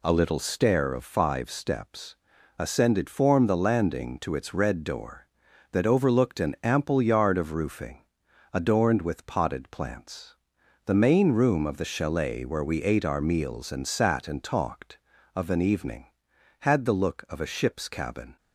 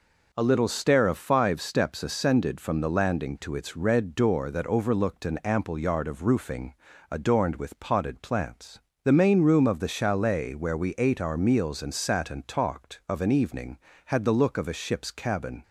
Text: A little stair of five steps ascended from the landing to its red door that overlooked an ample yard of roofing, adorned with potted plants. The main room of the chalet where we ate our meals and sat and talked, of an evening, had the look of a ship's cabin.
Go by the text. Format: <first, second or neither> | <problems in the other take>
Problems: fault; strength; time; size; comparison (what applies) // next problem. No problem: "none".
second | pauses between "steps" and "ascended"; at 2.1 s; 0.42 s long // says "form" for "from"; at 3.1 s